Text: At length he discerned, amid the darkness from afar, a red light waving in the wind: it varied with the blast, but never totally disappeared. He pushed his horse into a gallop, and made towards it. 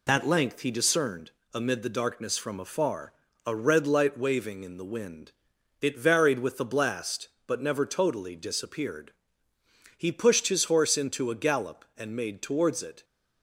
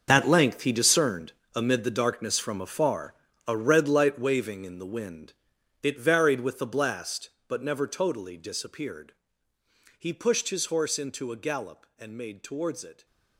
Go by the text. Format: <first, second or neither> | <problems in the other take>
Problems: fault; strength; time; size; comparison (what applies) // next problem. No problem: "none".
first | gets quieter; strong; throughout; 13 dB